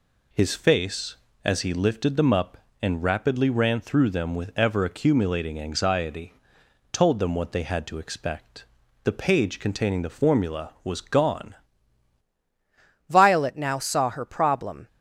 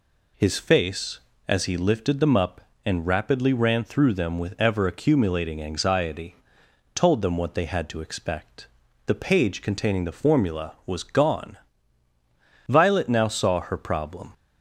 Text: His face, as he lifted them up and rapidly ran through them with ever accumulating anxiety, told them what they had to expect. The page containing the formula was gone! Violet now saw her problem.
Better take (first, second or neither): second